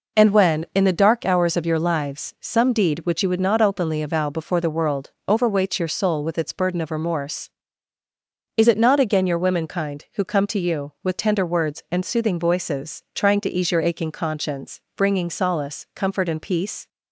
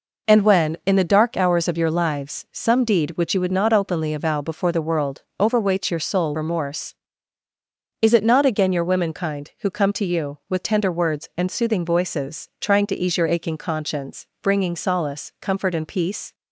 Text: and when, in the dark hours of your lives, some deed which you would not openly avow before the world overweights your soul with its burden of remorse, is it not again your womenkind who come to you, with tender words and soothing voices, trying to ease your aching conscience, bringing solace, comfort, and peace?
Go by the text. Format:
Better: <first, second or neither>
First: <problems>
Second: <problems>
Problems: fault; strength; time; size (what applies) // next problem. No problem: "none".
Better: first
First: pauses between "world" and "overweights"; slight; at 5.1 s; 0.16 s long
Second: pauses between "world" and "overweights"; slight; at 5.2 s; 0.16 s long // skips "with its burden of"; at 6.3 s